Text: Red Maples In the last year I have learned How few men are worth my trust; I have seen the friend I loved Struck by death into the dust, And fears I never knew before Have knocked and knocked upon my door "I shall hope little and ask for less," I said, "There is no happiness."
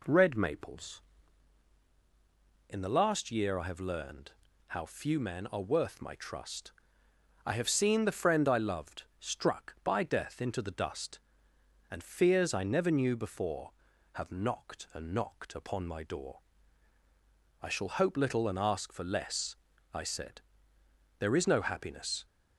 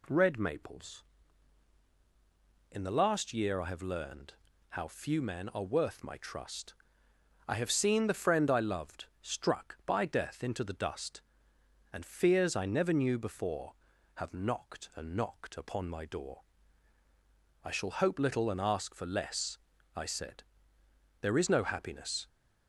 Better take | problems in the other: second | starts louder than the rest; slight; until 1.4 s; 3 dB // pauses between "learned" and "How"; slight; at 4.3 s; 0.34 s long; slight in the second // pauses between "loved" and "Struck"; slight; at 9.0 s; 0.18 s long; slight in the second // pauses between "door" and "I"; at 16.3 s; 1.2 s long; also in the second

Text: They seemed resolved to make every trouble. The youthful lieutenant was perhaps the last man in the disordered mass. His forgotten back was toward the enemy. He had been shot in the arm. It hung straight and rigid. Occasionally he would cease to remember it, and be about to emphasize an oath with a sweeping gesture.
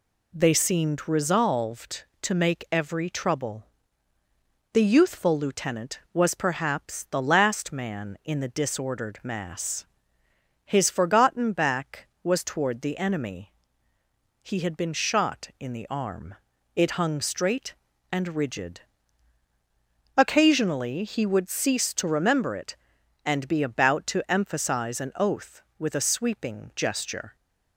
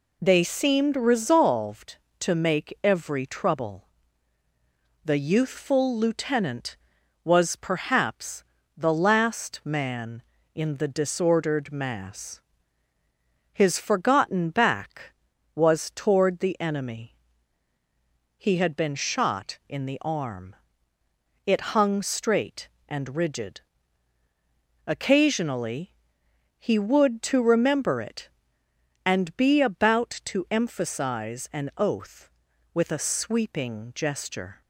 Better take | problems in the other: first | pauses between "perhaps" and "the"; slight; at 8.4 s; 0.34 s long // pauses between "Occasionally" and "he"; noticeable; at 25.9 s; 0.64 s long // skips "cease"; at 27.2 s

